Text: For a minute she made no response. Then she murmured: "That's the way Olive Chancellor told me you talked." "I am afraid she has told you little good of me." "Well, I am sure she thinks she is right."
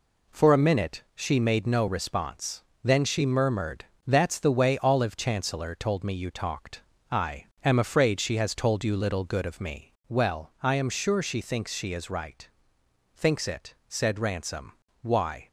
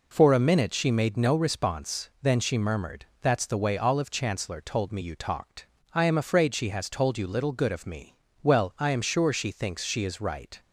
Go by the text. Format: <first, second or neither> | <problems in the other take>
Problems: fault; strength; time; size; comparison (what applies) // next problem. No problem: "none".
second | pauses between "I" and "am"; slight; at 7.4 s; 0.18 s long // goes on to say "Thinks it said Ransom Why"; strong; from 13.1 s on; 2.3 s long